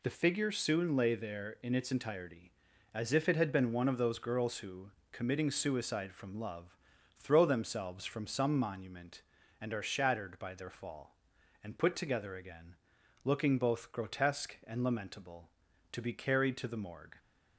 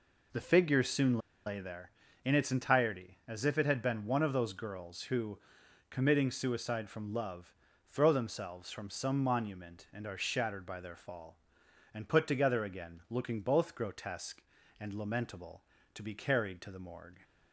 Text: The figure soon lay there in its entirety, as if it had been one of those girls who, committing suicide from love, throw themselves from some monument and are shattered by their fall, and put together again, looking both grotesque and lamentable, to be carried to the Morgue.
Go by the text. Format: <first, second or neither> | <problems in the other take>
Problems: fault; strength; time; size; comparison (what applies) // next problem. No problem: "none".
first | pauses between "soon" and "lay"; slight; at 1.1 s; 0.28 s long